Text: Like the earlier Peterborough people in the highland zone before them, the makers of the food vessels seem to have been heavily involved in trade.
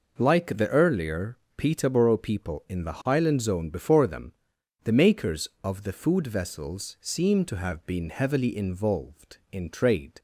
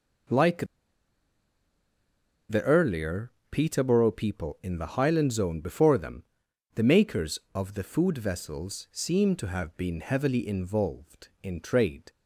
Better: first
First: pauses between "earlier" and "Peterborough"; slight; at 1.3 s; 0.22 s long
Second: pauses between "Like" and "the"; strong; at 0.6 s; 1.8 s long // pauses between "earlier" and "Peterborough"; slight; at 3.2 s; 0.22 s long

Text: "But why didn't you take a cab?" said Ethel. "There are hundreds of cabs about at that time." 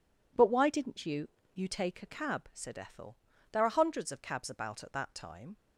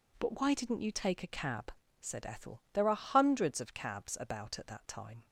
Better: second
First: says "you" twice; at 1.5 s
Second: none

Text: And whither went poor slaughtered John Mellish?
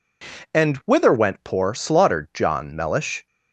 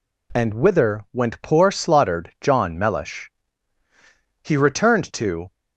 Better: first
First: none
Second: goes on to say "He returned to"; noticeable; from 4.4 s on; 1.1 s long

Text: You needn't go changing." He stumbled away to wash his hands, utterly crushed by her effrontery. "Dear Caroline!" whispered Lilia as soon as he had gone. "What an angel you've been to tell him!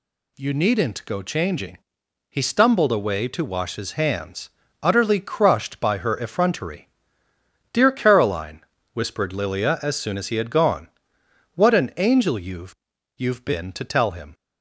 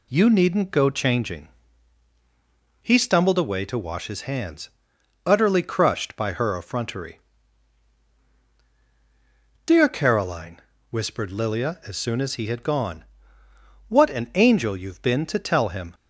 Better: second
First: says "you've" twice; at 13.1 s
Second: none

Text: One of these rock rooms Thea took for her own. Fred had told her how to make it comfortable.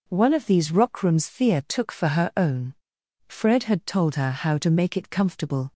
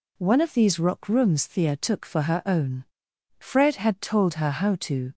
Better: first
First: none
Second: stops before "make it comfortable"; at 5.1 s

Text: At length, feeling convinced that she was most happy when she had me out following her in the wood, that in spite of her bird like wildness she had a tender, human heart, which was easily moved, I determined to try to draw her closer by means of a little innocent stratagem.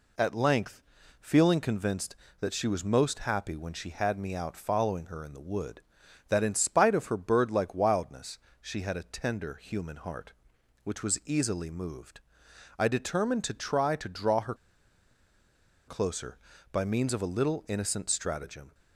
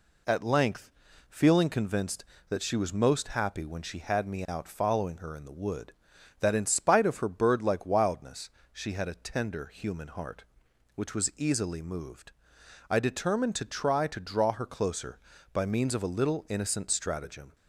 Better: second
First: pauses between "wildness" and "she"; slight; at 8.3 s; 0.24 s long // pauses between "her" and "closer"; strong; at 14.5 s; 1.3 s long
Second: pauses between "wildness" and "she"; slight; at 8.4 s; 0.24 s long

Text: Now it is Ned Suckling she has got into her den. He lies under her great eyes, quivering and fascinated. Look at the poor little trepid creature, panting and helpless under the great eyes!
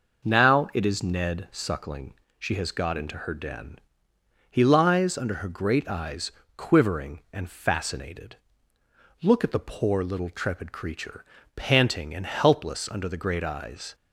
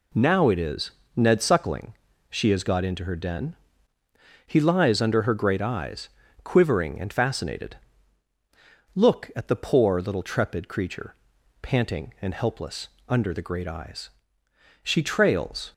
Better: first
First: pauses between "Suckling" and "she"; slight; at 2.1 s; 0.26 s long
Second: pauses between "is" and "Ned"; slight; at 0.9 s; 0.26 s long // pauses between "Suckling" and "she"; slight; at 1.9 s; 0.34 s long // pauses between "helpless" and "under"; slight; at 12.8 s; 0.20 s long // goes on to say "She trails"; noticeable; from 14.8 s on; 0.90 s long

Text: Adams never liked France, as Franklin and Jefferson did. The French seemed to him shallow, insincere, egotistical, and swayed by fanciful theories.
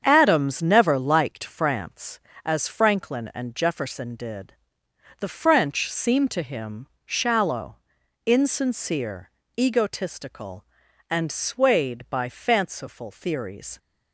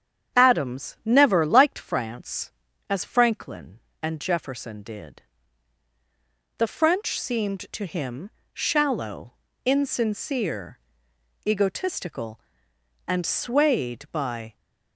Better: first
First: starts louder than the rest; strong; until 1.0 s; 7.5 dB // pauses between "him" and "shallow"; slight; at 6.8 s; 0.18 s long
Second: starts louder than the rest; strong; until 1.4 s; 8.5 dB // pauses between "him" and "shallow"; slight; at 8.3 s; 0.20 s long // stops before "fanciful theories"; at 14.5 s

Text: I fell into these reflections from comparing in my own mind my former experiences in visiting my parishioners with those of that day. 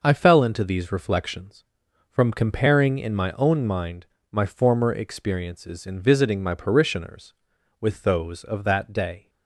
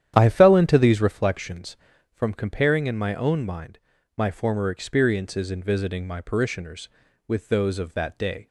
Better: first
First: pauses between "mind" and "my"; slight; at 4.0 s; 0.26 s long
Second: starts louder than the rest; strong; until 1.2 s; 10 dB // pauses between "mind" and "my"; at 3.7 s; 0.38 s long

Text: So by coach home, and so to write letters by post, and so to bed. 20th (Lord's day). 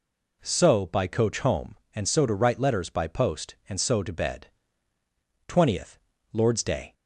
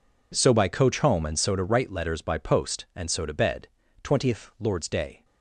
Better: neither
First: none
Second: none

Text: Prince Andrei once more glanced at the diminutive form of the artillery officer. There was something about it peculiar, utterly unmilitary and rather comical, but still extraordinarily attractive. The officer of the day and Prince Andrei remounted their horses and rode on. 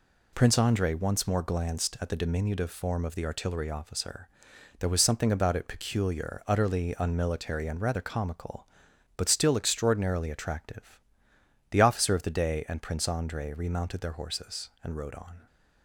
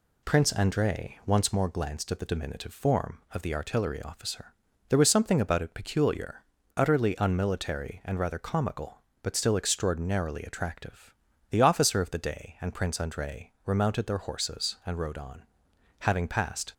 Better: first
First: none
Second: goes on to say "Having passed"; noticeable; from 15.9 s on; 0.74 s long

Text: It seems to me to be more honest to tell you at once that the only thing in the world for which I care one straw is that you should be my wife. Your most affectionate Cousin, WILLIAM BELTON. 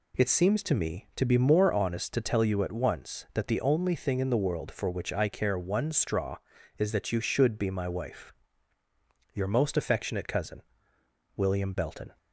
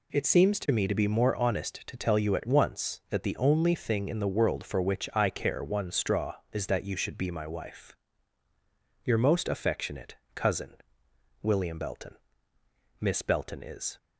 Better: first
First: none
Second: pauses between "affectionate" and "Cousin"; slight; at 10.1 s; 0.20 s long // goes on to say "Miss Belton is"; noticeable; from 13.0 s on; 0.96 s long

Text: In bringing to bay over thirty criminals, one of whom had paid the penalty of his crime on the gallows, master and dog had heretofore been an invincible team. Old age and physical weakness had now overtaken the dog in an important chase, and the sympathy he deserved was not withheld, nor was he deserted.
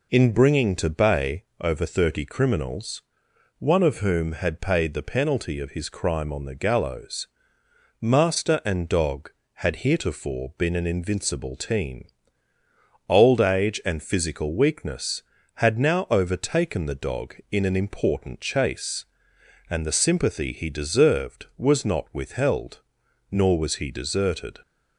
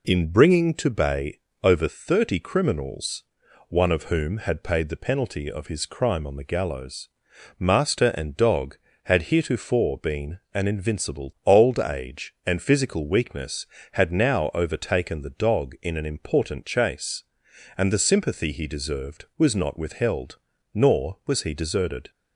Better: first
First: pauses between "bay" and "over"; slight; at 1.4 s; 0.18 s long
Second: pauses between "bay" and "over"; slight; at 1.3 s; 0.24 s long // pauses between "been" and "an"; slight; at 10.3 s; 0.16 s long // skips "team"; at 11.3 s

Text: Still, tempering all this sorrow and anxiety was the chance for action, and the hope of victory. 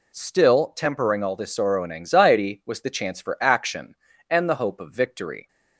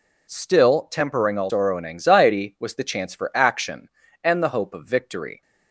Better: first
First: none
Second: skips "this"; at 1.4 s

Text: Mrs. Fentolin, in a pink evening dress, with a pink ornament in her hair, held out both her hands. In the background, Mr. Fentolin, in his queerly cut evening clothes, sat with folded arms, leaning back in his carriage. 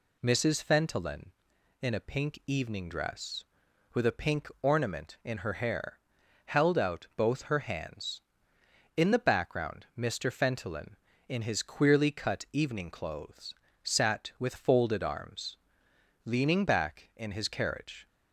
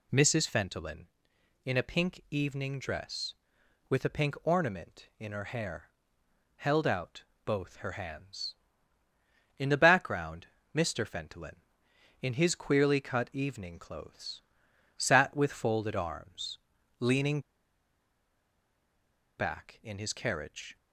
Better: first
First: none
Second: pauses between "out" and "both"; slight; at 7.2 s; 0.22 s long // pauses between "leaning" and "back"; strong; at 17.4 s; 1.9 s long

